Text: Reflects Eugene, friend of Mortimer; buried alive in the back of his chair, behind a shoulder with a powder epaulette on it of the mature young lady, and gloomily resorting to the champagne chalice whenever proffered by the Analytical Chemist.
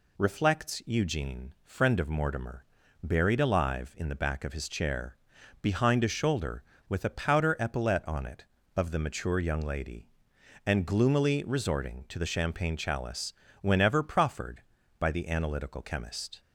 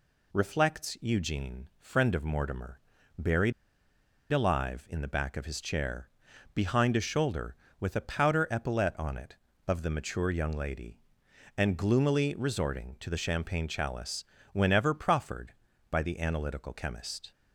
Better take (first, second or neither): first